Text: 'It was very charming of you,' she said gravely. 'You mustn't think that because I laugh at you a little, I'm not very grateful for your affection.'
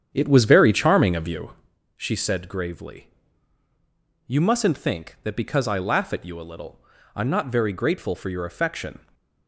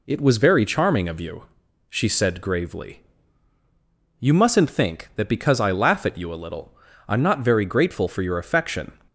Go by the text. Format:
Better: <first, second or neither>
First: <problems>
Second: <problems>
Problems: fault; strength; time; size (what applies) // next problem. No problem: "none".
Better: second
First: starts louder than the rest; strong; until 1.8 s; 8.5 dB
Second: none